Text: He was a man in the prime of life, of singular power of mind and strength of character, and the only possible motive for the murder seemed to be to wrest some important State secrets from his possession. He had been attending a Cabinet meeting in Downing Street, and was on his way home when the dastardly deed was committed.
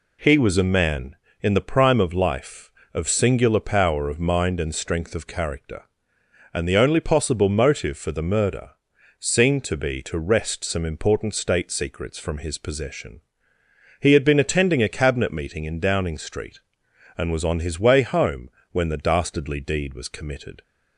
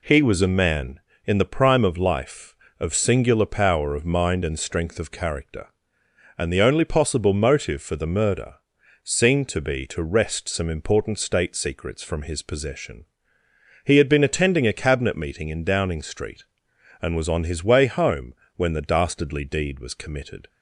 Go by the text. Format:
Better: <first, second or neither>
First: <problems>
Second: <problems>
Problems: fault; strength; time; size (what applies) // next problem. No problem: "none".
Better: neither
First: pauses between "murder" and "seemed"; noticeable; at 8.6 s; 0.50 s long // pauses between "home" and "when"; slight; at 18.4 s; 0.22 s long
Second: pauses between "murder" and "seemed"; noticeable; at 8.5 s; 0.50 s long // pauses between "home" and "when"; slight; at 18.3 s; 0.22 s long